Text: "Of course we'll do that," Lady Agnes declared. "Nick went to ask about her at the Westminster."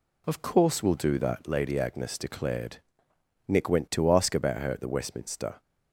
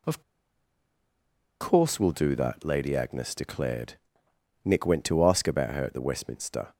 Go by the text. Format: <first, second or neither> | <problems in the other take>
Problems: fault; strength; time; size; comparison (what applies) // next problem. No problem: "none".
first | pauses between "Of" and "course"; strong; at 0.2 s; 1.3 s long